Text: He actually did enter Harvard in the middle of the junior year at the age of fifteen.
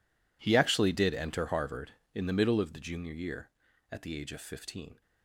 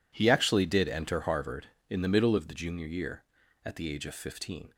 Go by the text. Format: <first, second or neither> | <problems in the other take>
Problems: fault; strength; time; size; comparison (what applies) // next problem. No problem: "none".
second | gets quieter; strong; throughout; 19.5 dB